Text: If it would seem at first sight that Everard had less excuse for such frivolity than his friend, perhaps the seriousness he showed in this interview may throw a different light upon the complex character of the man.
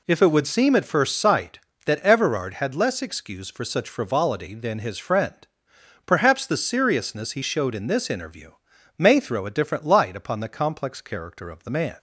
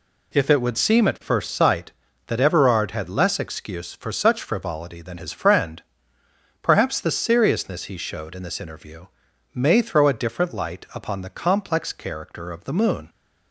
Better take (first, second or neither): first